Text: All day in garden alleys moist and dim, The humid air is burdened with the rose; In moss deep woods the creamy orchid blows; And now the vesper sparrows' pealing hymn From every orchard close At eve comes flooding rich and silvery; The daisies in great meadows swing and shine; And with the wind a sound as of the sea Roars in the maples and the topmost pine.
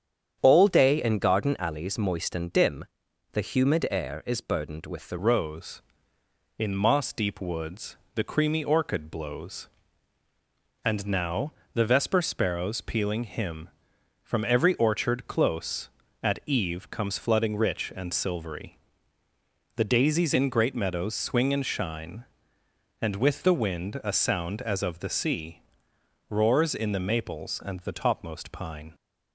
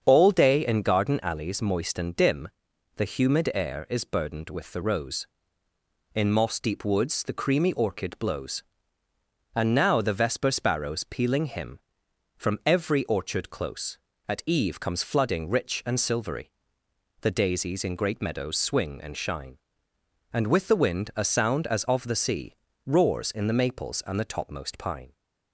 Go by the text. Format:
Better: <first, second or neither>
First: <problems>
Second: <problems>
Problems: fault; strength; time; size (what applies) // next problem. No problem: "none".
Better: second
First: starts louder than the rest; strong; until 1.4 s; 8.5 dB // changes voice at "rose"; from 5.1 s on; 23.8 s long // pauses between "woods" and "the"; slight; at 7.9 s; 0.20 s long // pauses between "now" and "the"; slight; at 11.5 s; 0.22 s long // pauses between "sea" and "Roars"; noticeable; at 25.6 s; 0.68 s long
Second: starts louder than the rest; strong; until 1.0 s; 7.5 dB // pauses between "sea" and "Roars"; slight; at 22.5 s; 0.32 s long